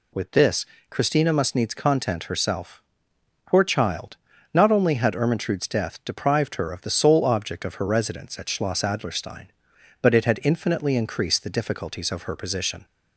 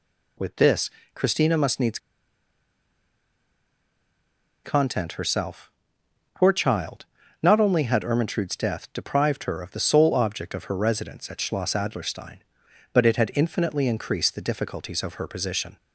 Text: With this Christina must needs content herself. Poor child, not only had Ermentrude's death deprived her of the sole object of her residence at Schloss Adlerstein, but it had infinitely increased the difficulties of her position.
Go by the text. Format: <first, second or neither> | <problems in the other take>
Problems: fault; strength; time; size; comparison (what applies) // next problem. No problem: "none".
first | pauses between "this" and "Christina"; slight; at 0.8 s; 0.26 s long; slight in the first // pauses between "needs" and "content"; strong; at 1.9 s; 2.6 s long